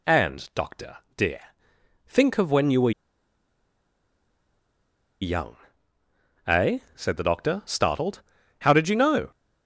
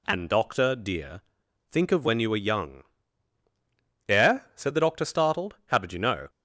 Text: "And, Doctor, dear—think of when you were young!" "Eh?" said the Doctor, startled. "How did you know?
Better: second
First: pauses between "were" and "young"; strong; at 2.9 s; 2.3 s long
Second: none

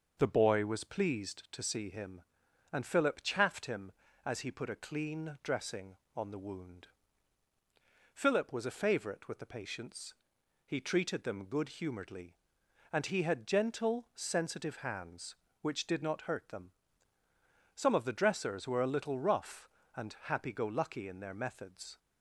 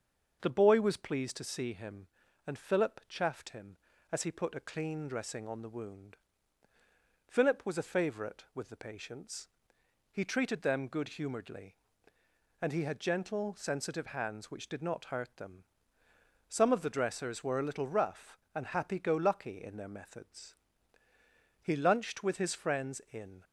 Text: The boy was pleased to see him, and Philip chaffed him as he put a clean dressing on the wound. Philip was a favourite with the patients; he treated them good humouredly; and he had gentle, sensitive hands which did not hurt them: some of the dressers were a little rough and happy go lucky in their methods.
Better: first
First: starts louder than the rest; noticeable; until 1.2 s; 6 dB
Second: starts louder than the rest; until 1.4 s; 6.5 dB // goes on to say "He lunched with his friends in"; strong; from 21.6 s on; 1.8 s long

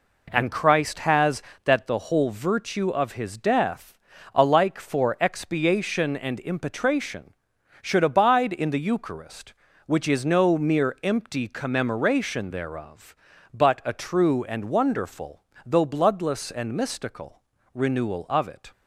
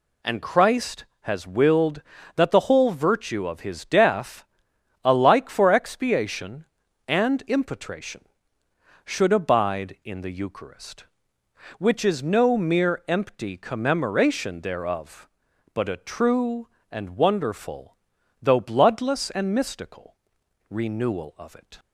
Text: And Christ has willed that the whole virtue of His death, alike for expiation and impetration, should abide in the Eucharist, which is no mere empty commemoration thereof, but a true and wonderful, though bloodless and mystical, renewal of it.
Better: second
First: skips "willed"; at 1.5 s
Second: none

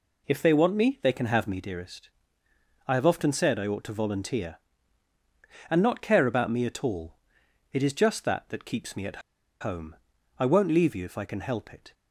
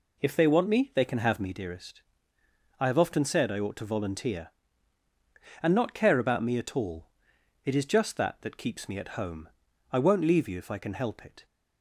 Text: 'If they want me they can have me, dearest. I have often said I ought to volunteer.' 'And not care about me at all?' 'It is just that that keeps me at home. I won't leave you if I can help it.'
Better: second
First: pauses between "at" and "home"; at 9.2 s; 0.41 s long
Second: none

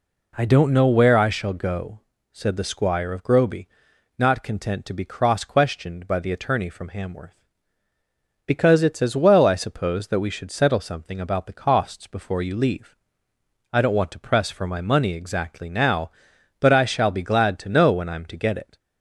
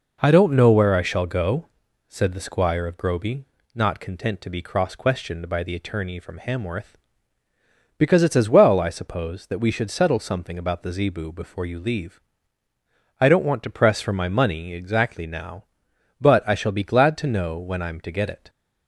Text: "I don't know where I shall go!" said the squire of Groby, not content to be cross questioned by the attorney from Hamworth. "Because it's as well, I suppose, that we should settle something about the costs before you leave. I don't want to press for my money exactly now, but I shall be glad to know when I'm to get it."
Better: first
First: none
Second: says "zebu" for "costs"; at 10.9 s

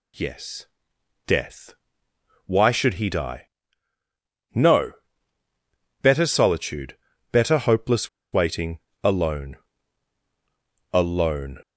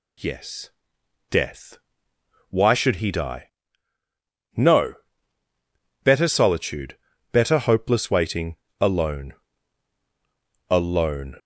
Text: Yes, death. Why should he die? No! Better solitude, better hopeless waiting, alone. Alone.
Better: second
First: pauses between "hopeless" and "waiting"; slight; at 8.0 s; 0.26 s long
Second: none

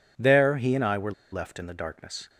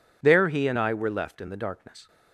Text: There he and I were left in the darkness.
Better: second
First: pauses between "were" and "left"; slight; at 1.1 s; 0.20 s long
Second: none

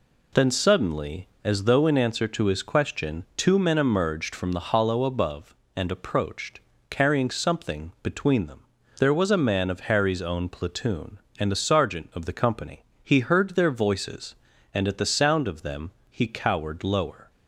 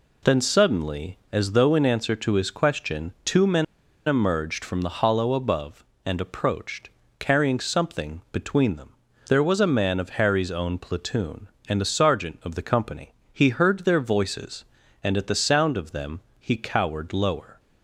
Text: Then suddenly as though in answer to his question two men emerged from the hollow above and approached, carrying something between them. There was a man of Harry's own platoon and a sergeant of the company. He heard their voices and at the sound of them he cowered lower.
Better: first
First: pauses between "them" and "he"; slight; at 15.9 s; 0.18 s long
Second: pauses between "men" and "emerged"; at 3.6 s; 0.42 s long // pauses between "them" and "he"; slight; at 16.2 s; 0.18 s long

